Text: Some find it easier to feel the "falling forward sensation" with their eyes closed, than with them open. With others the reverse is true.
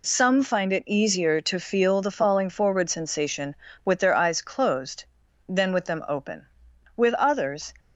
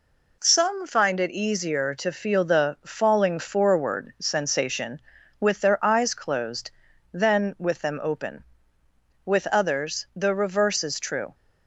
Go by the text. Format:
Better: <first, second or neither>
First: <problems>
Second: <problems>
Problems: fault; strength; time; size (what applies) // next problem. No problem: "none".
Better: second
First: stops before "the reverse is true"; at 7.7 s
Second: none